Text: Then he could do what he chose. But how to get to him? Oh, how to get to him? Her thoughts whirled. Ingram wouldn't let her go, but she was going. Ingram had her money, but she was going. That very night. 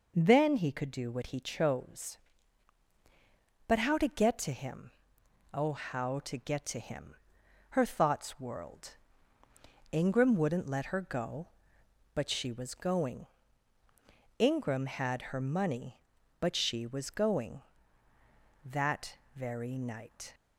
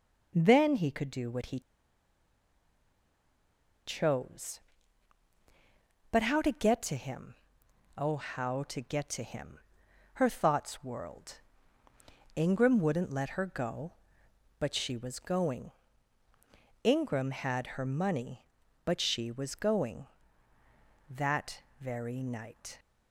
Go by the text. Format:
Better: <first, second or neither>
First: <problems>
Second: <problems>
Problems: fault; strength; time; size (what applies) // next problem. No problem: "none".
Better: first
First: pauses between "That" and "very"; slight; at 19.1 s; 0.18 s long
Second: pauses between "he" and "chose"; strong; at 1.5 s; 2.2 s long // pauses between "That" and "very"; slight; at 21.6 s; 0.18 s long